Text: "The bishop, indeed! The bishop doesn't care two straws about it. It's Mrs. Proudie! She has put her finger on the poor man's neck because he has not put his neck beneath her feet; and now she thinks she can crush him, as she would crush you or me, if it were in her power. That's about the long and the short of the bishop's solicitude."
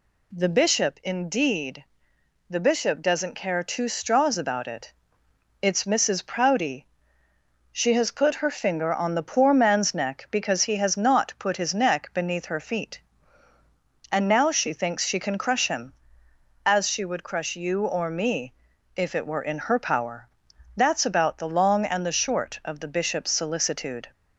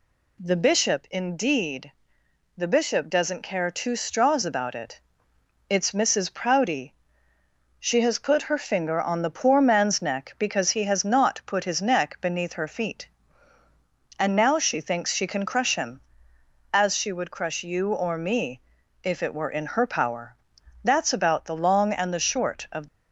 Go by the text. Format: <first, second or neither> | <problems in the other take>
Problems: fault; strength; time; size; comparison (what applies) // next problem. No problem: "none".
first | stops before "the bishop's solicitude"; at 22.8 s